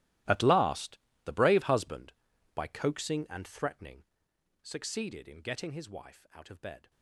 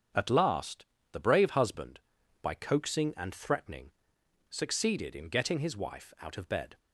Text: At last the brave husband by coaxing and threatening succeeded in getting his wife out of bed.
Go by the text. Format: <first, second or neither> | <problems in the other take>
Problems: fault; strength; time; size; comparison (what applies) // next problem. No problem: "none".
second | gets quieter; strong; throughout; 18.5 dB // starts louder than the rest; strong; until 1.5 s; 15.5 dB; strong in the second // pauses between "last" and "the"; slight; at 0.9 s; 0.26 s long; slight in the second // pauses between "threatening" and "succeeded"; noticeable; at 4.0 s; 0.58 s long; noticeable in the second